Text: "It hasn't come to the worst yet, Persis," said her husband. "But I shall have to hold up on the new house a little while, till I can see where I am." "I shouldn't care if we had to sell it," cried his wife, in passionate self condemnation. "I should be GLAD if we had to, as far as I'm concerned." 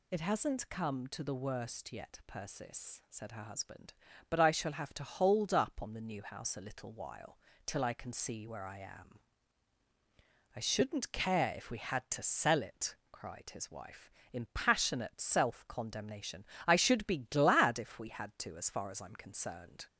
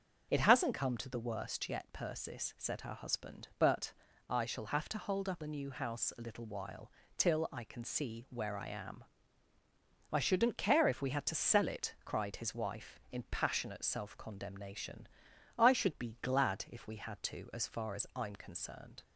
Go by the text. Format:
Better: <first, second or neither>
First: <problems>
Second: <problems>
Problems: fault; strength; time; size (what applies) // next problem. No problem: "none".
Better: first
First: none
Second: starts louder than the rest; until 1.3 s; 6.5 dB // pauses between "But" and "I"; slight; at 3.9 s; 0.34 s long // skips "on"; at 5.4 s